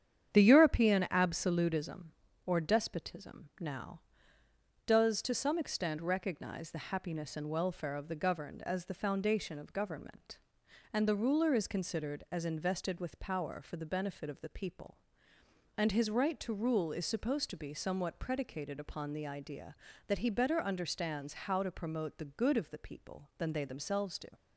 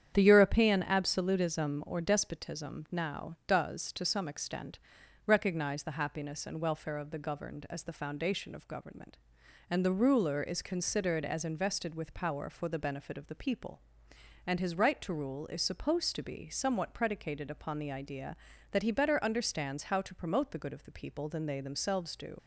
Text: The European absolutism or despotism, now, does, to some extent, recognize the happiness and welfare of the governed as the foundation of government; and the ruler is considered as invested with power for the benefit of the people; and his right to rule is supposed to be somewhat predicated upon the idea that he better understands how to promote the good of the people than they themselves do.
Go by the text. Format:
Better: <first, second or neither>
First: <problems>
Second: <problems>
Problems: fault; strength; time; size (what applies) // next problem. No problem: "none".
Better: first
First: starts louder than the rest; strong; until 1.3 s; 9 dB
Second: starts louder than the rest; strong; until 1.1 s; 9 dB // leaves "do" unfinished; at 22.3 s; 50 ms